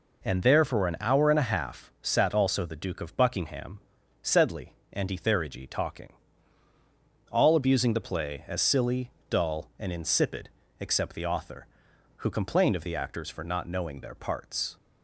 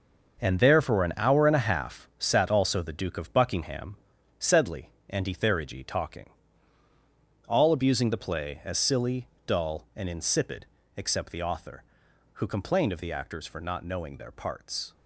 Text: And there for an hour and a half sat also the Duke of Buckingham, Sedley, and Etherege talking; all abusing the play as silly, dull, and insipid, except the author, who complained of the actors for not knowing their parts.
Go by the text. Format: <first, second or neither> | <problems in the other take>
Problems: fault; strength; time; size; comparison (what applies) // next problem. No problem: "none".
first | gets quieter; strong; throughout; 9.5 dB